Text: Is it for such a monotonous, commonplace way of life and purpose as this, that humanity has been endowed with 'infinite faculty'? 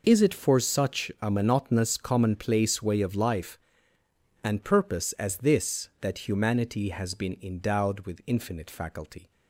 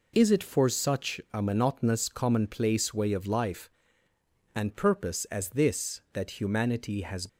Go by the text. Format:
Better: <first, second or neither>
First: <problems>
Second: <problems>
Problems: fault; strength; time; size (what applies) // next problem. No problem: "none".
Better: first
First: none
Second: stops before "been endowed with infinite faculty"; at 7.2 s